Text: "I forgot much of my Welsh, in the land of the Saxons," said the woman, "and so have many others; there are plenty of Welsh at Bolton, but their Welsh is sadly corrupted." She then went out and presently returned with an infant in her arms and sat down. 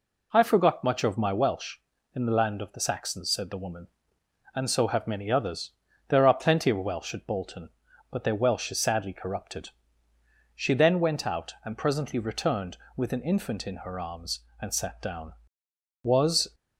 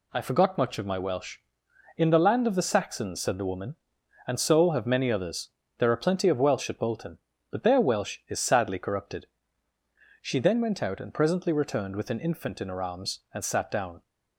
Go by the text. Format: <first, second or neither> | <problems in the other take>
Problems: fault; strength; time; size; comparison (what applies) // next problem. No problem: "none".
second | goes on to say "Was"; from 16.0 s on; 0.52 s long